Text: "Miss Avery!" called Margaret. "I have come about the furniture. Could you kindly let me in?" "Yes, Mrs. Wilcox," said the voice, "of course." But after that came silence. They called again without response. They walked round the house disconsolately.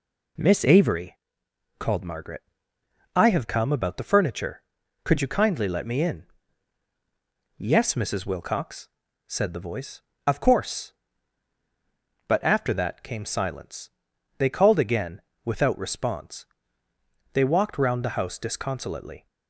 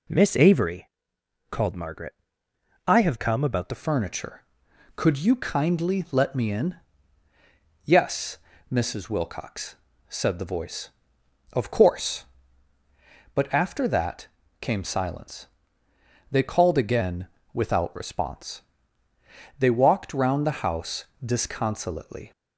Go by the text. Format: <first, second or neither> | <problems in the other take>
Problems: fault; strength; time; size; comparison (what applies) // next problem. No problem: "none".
first | changes voice at "furniture"; from 3.7 s on; 18.6 s long // pauses between "that" and "came"; slight; at 14.2 s; 0.32 s long // pauses between "again" and "without"; slight; at 17.2 s; 0.26 s long; slight in the first // pauses between "house" and "disconsolately"; slight; at 21.0 s; 0.18 s long